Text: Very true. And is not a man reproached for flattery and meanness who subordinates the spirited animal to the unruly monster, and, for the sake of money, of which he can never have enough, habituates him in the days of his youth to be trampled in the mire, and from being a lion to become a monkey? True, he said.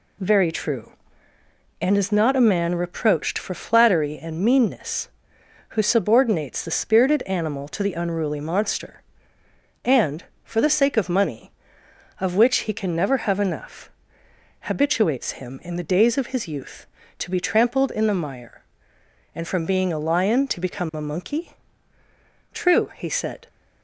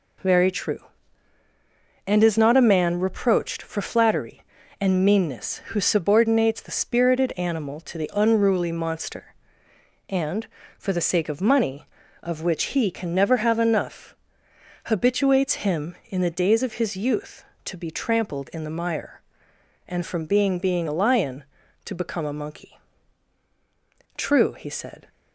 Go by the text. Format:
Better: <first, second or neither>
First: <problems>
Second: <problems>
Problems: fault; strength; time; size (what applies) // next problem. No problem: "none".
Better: first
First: none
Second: says "being" twice; at 20.5 s